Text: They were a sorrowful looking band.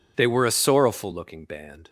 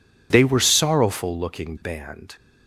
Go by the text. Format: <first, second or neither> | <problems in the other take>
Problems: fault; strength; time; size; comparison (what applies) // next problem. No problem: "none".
first | skips "a"; at 0.6 s